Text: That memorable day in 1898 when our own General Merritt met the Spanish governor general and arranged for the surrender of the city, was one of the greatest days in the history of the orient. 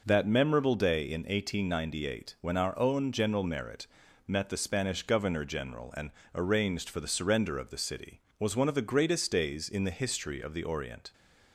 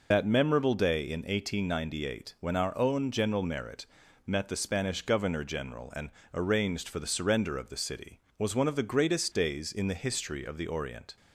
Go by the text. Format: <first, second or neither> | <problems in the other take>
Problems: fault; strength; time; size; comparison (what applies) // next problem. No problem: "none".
first | loses the start of "That"; at 0.1 s; 55 ms // pauses between "Merritt" and "met"; at 3.8 s; 0.40 s long; also in the first // pauses between "and" and "arranged"; slight; at 6.0 s; 0.24 s long; slight in the first